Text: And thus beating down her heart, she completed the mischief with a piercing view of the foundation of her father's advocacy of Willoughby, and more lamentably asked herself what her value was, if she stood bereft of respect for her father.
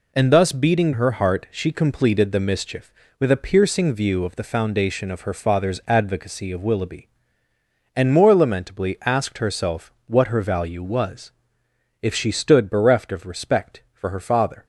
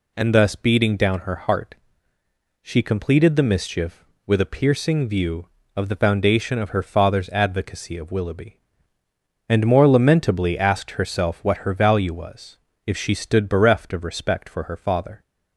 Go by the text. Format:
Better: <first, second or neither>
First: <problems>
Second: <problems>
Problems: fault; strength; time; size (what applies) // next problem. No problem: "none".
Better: second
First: skips "down"; at 0.9 s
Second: none